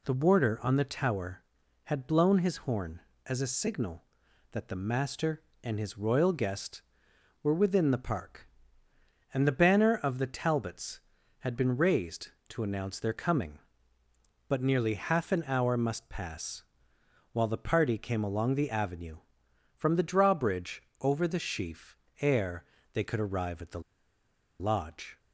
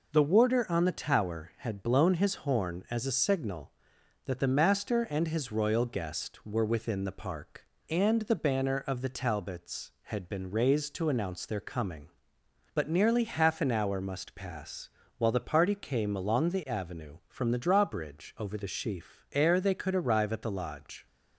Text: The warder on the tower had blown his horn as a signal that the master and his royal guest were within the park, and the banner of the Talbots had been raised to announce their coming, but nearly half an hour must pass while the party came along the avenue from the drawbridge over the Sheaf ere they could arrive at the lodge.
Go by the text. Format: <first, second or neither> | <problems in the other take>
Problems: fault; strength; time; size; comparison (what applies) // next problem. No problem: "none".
second | pauses between "pass" and "while"; noticeable; at 16.6 s; 0.68 s long; slight in the second // pauses between "drawbridge" and "over"; slight; at 20.8 s; 0.18 s long // pauses between "Sheaf" and "ere"; slight; at 21.9 s; 0.24 s long // pauses between "ere" and "they"; slight; at 22.6 s; 0.26 s long // pauses between "the" and "lodge"; noticeable; at 23.7 s; 0.79 s long